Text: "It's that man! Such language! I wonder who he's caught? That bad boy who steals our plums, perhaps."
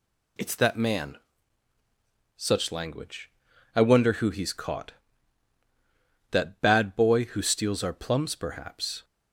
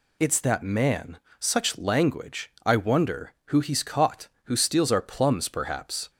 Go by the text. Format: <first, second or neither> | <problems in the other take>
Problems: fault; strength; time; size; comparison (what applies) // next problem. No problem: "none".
first | skips "That bad boy"; at 4.3 s